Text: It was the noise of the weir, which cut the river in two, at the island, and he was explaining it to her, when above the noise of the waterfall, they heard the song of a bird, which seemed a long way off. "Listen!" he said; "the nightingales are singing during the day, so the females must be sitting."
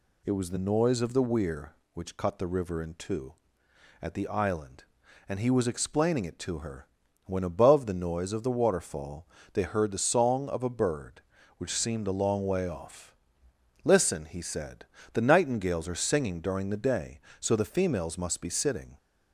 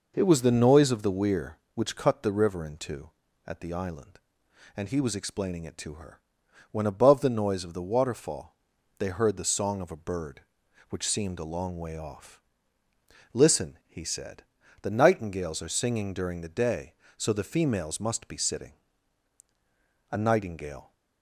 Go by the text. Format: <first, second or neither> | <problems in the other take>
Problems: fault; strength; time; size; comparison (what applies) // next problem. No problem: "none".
first | goes on to say "A nightingale"; noticeable; from 20.1 s on; 0.82 s long